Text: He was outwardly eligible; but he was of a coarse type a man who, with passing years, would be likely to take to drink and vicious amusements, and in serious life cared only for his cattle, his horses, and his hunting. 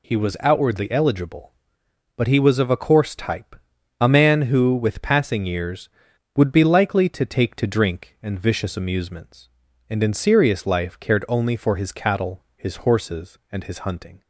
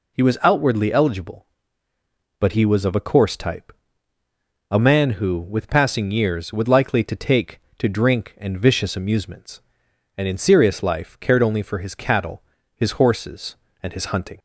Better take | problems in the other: first | pauses between "type" and "a"; noticeable; at 3.7 s; 0.98 s long; also in the first // skips "be"; at 6.6 s

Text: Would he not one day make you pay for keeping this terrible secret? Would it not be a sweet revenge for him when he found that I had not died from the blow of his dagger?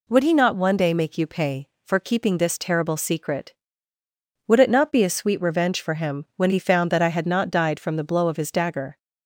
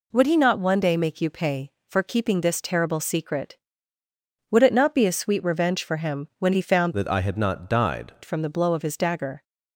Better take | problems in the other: first | changes voice from "that" to "died"; from 6.9 to 8.1 s; 1.2 s long

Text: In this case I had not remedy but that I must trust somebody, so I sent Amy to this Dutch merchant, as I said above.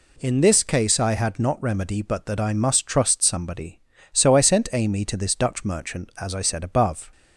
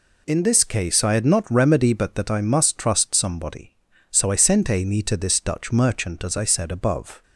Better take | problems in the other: neither | none

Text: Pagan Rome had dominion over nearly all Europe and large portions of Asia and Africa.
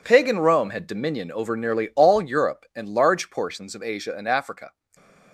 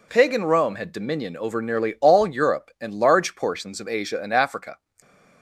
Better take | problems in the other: second | gets quieter; strong; throughout; 11 dB // stays silent after the last word; slight; from 4.6 s on; 0.7 s long

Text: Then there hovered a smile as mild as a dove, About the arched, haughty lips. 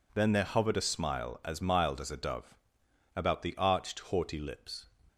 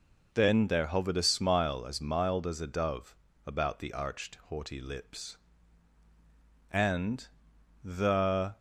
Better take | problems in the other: first | goes on to say "And the"; strong; from 6.6 s on; 1.8 s long

